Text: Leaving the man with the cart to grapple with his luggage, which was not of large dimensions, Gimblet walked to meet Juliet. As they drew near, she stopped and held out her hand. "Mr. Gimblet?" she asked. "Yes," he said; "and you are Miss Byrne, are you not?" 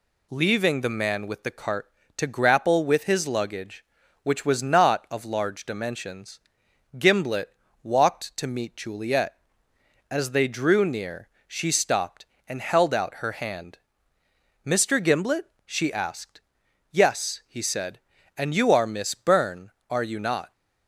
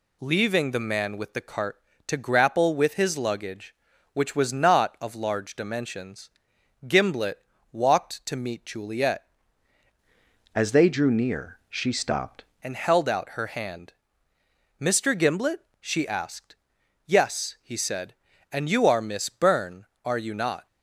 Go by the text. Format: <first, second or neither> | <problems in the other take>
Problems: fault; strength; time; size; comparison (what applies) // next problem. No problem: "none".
first | pauses between "Gimblet" and "walked"; slight; at 7.3 s; 0.34 s long; slight in the first // changes voice from "As" to "stopped"; from 10.5 to 12.4 s; 1.9 s long